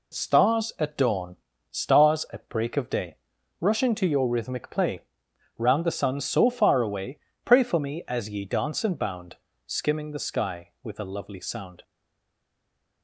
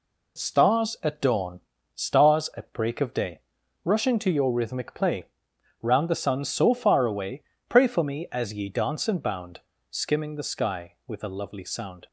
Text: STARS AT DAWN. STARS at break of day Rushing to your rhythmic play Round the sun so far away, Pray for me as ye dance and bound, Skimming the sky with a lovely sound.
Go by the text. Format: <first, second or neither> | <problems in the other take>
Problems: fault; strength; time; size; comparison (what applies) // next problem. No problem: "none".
second | pauses between "day" and "Rushing"; noticeable; at 3.1 s; 0.46 s long; noticeable in the second // pauses between "play" and "Round"; noticeable; at 5.0 s; 0.56 s long; noticeable in the second // stays silent after the last word; noticeable; from 11.8 s on; 1.2 s long